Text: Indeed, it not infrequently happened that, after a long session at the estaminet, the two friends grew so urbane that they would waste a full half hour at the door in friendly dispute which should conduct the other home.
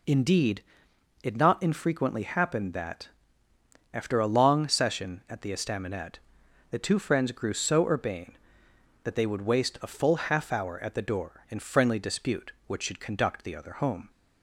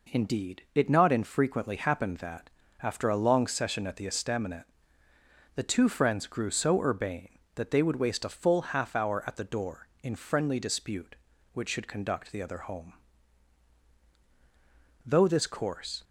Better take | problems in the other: first | goes on to say "Though this course"; noticeable; from 15.0 s on; 0.98 s long

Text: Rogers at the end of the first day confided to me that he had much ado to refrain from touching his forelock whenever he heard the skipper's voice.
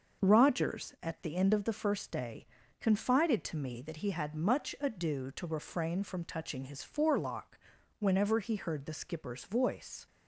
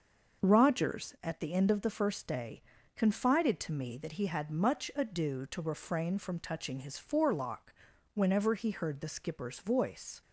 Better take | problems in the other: neither | starts louder than the rest; the same in both // pauses between "day" and "confided"; slight; the same in both // pauses between "forelock" and "whenever"; the same in both

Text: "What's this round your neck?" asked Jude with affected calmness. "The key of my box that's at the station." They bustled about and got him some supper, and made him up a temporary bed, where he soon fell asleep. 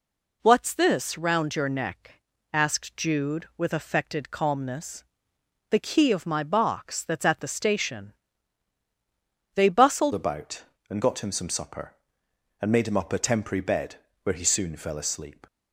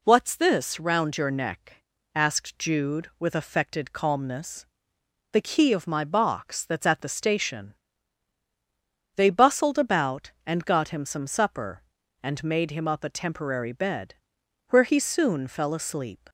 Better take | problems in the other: second | changes voice at "about"; from 10.1 s on; 5.3 s long

